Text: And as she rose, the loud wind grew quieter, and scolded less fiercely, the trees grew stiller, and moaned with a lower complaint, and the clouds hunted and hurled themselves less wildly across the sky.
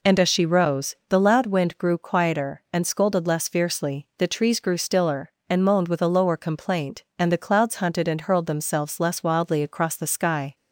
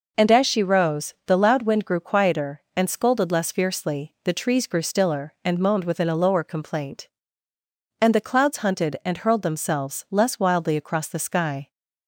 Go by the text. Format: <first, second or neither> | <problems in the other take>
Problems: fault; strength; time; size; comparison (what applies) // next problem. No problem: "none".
first | says "within" for "with"; at 5.8 s